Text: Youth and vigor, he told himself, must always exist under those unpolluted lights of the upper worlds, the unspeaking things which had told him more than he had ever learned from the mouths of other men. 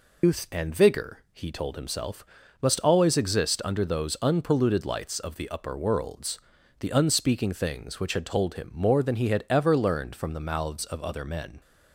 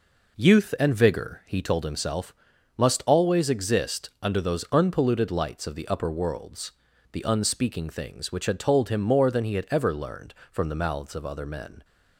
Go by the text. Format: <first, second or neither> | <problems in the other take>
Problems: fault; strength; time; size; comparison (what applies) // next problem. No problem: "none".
second | loses the start of "Youth"; at 0.2 s; 110 ms